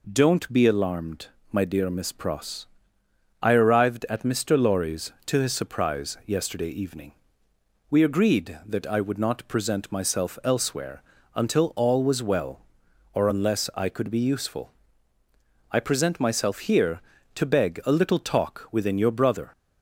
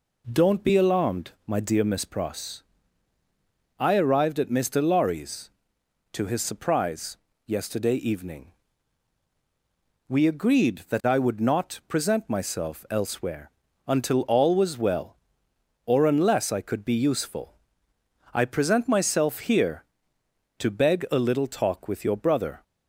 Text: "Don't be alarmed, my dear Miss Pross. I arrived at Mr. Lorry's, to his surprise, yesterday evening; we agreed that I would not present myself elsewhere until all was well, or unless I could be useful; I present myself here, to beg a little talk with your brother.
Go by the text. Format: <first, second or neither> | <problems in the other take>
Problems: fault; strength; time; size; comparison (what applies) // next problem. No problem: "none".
second | pauses between "elsewhere" and "until"; slight; at 11.0 s; 0.32 s long; also in the second // says "within" for "with"; at 18.6 s